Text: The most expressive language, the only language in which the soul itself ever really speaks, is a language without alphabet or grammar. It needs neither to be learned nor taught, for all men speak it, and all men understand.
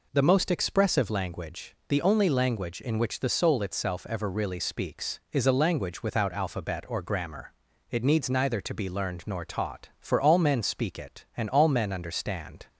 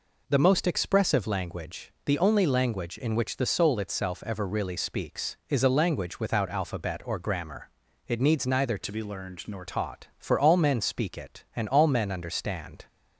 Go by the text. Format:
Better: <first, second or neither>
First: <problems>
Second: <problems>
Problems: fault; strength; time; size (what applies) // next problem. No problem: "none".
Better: first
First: none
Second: changes voice from "to" to "nor"; from 8.8 to 9.6 s; 0.8 s long